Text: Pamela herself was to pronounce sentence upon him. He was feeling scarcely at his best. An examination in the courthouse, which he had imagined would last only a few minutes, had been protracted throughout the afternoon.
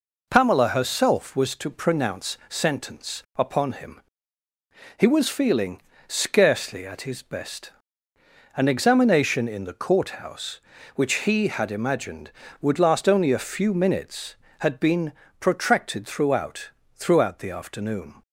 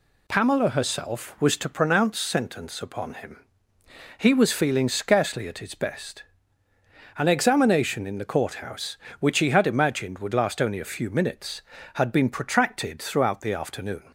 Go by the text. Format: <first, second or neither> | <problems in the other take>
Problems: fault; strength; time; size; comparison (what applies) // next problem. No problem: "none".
second | pauses between "feeling" and "scarcely"; slight; at 5.7 s; 0.26 s long // pauses between "been" and "protracted"; slight; at 15.1 s; 0.26 s long // says "throughout" twice; at 16.9 s